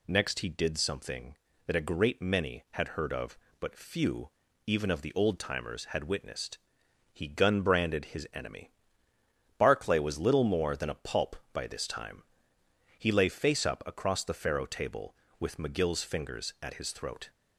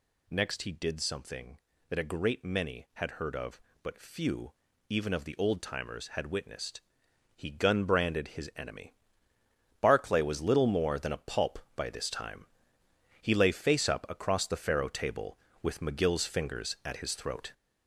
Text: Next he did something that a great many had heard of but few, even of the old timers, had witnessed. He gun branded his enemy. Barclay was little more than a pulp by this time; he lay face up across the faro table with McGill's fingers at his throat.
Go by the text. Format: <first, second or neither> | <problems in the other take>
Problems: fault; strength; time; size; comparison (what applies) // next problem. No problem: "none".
first | gets louder; noticeable; throughout; 5.5 dB